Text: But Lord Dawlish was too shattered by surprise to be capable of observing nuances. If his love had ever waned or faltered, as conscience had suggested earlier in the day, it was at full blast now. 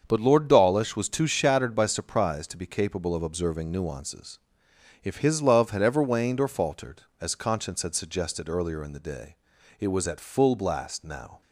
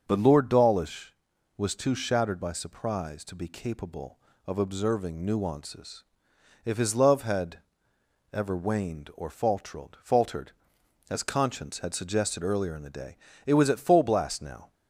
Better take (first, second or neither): first